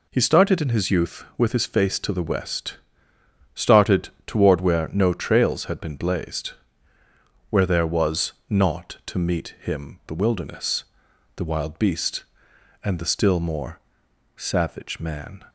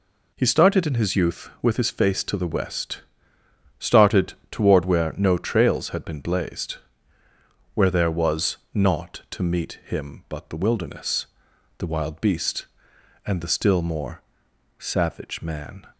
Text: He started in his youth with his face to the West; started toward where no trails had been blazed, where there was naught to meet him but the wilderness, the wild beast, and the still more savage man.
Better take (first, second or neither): second